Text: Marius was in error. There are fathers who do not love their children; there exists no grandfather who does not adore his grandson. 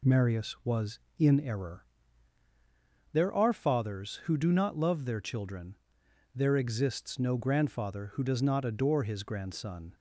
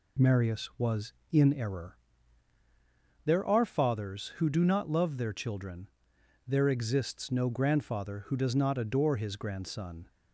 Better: neither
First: none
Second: none

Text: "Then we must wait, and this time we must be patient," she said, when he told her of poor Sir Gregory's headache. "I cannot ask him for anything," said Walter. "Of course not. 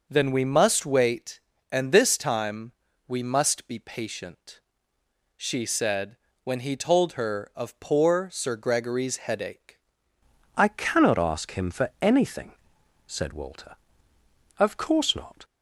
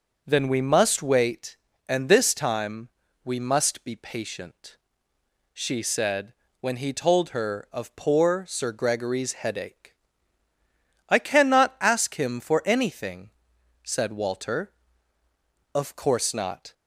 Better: second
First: pauses between "time" and "we"; at 2.7 s; 0.38 s long // changes voice at "I"; from 10.5 s on; 4.9 s long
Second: pauses between "time" and "we"; at 2.8 s; 0.38 s long

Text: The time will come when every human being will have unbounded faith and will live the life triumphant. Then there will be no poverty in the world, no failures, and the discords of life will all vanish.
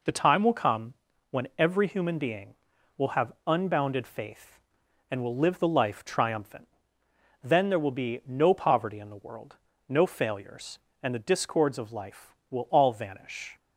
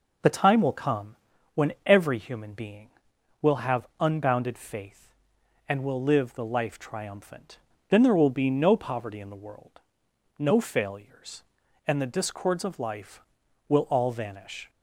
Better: neither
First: pauses between "come" and "when"; slight; at 0.9 s; 0.36 s long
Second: pauses between "come" and "when"; at 1.1 s; 0.40 s long

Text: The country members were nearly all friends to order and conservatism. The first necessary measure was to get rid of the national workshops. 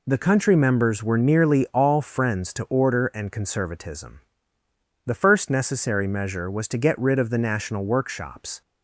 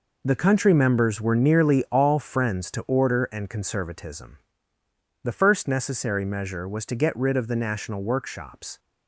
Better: first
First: none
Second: gets quieter; strong; throughout; 9.5 dB

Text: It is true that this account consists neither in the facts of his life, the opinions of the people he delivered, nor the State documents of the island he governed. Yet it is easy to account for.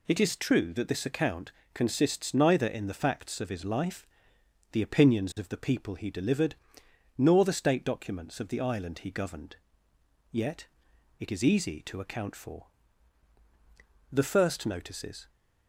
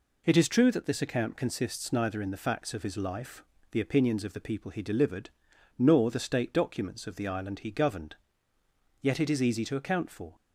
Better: second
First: pauses between "account" and "consists"; slight; at 1.5 s; 0.22 s long // pauses between "Yet" and "it"; noticeable; at 10.6 s; 0.54 s long // goes on to say "The first notices"; noticeable; from 14.1 s on; 1.1 s long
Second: none

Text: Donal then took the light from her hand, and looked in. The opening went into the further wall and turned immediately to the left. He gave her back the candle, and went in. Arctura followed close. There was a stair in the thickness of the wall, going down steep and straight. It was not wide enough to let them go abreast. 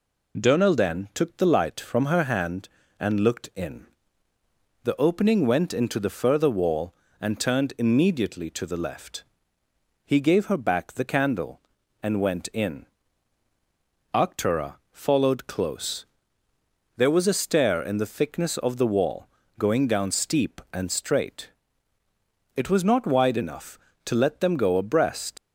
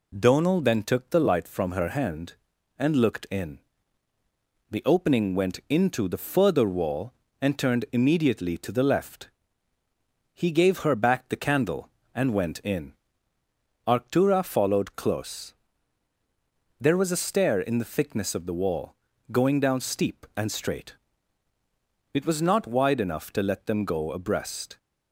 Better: second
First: pauses between "Arctura" and "followed"; slight; at 14.7 s; 0.16 s long // leaves "abreast" unfinished; at 25.3 s; 85 ms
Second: none

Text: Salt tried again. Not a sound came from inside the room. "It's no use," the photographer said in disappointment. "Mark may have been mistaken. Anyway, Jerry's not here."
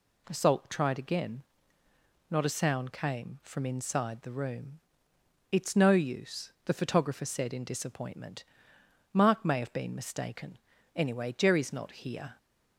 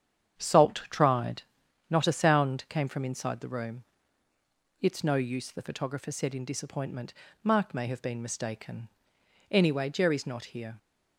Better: first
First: none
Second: starts louder than the rest; strong; until 1.9 s; 8.5 dB // skips "again"; at 1.6 s

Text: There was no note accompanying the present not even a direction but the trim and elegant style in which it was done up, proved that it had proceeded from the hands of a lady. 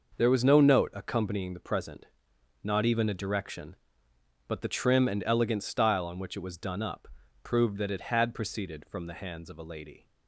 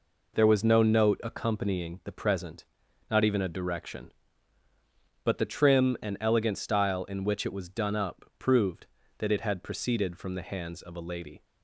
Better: second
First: pauses between "present" and "not"; noticeable; at 2.0 s; 0.58 s long // says "on" for "in"; at 6.0 s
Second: pauses between "present" and "not"; at 2.6 s; 0.44 s long

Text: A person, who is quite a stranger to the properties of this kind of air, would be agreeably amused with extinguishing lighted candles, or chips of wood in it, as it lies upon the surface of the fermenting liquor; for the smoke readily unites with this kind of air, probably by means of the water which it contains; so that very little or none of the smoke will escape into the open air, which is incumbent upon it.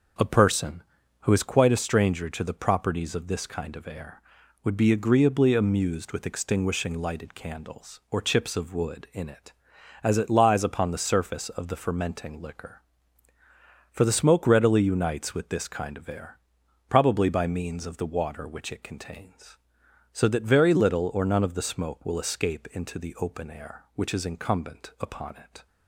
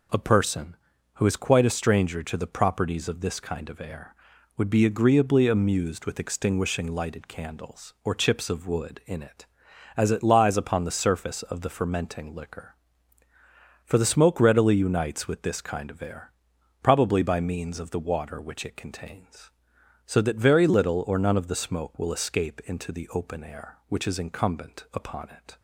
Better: second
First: starts louder than the rest; noticeable; until 1.6 s; 5.5 dB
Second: none

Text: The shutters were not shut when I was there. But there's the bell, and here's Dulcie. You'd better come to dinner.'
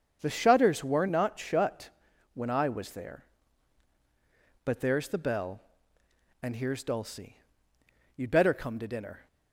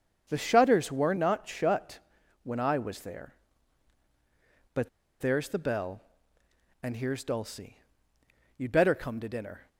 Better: first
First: starts louder than the rest; until 1.2 s; 7 dB // pauses between "shut" and "when"; at 1.8 s; 0.44 s long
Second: starts louder than the rest; until 1.2 s; 7 dB // pauses between "shut" and "when"; at 1.9 s; 0.44 s long // pauses between "But" and "there's"; slight; at 4.8 s; 0.31 s long

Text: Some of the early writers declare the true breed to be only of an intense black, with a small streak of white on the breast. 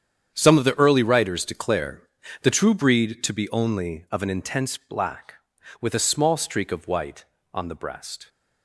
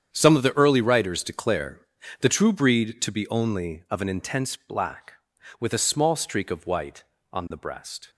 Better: neither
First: starts louder than the rest; strong; until 1.3 s; 8.5 dB // pauses between "declare" and "the"; at 2.0 s; 0.40 s long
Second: starts louder than the rest; strong; until 1.1 s; 8.5 dB // pauses between "declare" and "the"; at 1.7 s; 0.40 s long

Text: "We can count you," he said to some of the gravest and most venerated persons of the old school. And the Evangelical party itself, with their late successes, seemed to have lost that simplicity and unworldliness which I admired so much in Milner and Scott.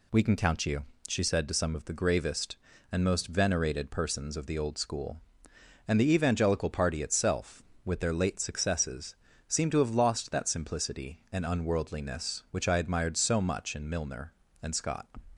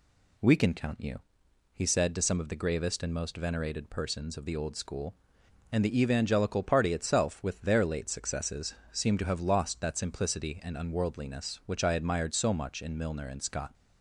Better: second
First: says "she" for "he"; at 1.0 s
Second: none

